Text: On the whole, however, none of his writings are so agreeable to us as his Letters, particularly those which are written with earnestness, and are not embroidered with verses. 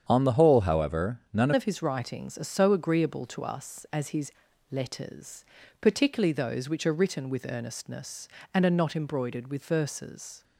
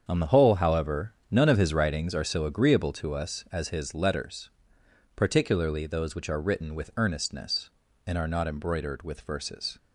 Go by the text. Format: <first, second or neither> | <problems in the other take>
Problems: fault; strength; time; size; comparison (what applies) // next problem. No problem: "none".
second | starts louder than the rest; strong; until 1.1 s; 8 dB; strong in the second // changes voice at "of"; from 1.5 s on; 8.9 s long // pauses between "his" and "Letters"; at 4.3 s; 0.40 s long